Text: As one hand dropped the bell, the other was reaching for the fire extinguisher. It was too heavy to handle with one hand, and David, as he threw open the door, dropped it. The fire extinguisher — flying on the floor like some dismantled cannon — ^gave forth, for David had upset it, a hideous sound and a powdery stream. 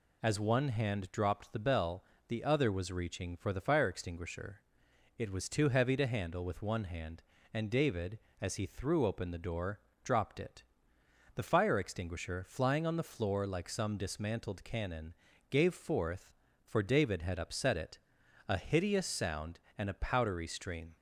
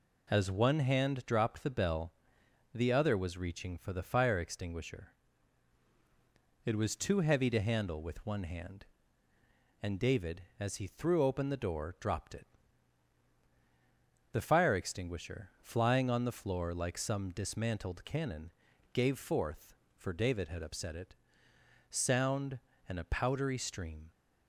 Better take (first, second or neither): first